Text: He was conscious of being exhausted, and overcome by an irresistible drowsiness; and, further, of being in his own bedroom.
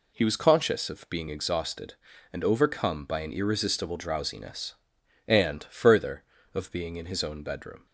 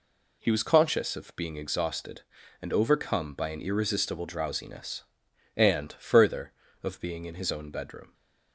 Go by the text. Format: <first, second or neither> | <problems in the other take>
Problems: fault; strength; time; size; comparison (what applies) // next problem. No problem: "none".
neither | none